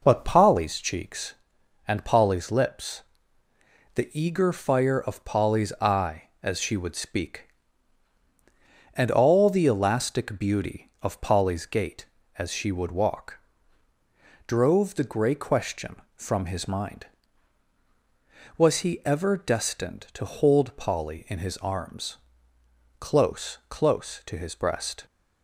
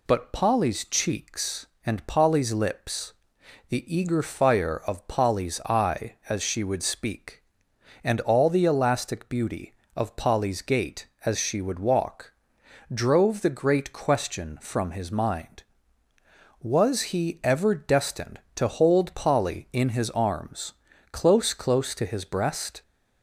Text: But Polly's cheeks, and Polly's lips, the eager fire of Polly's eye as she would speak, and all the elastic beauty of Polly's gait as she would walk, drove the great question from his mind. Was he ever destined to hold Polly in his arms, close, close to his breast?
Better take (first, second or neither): second